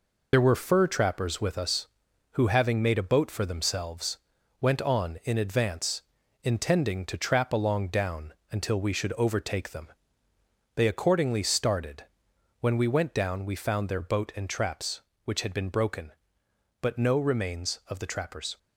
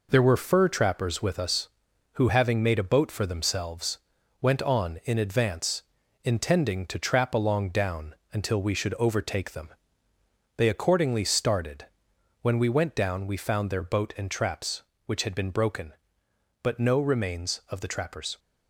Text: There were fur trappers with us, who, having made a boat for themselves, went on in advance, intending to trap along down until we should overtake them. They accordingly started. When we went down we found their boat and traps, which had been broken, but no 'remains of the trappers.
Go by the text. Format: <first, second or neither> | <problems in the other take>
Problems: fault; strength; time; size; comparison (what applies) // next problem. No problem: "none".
second | loses the start of "There"; at 0.3 s; 55 ms // pauses between "down" and "until"; slight; at 8.3 s; 0.18 s long; slight in the second